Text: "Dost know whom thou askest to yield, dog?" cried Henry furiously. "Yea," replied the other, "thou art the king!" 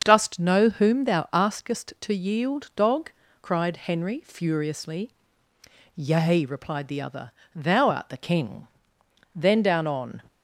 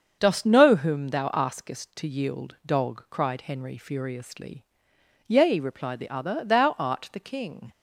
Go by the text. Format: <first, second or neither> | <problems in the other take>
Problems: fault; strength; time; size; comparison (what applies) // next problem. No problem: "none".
second | starts louder than the rest; until 1.0 s; 6.5 dB; also in the second // goes on to say "Then down on"; noticeable; from 9.3 s on; 0.88 s long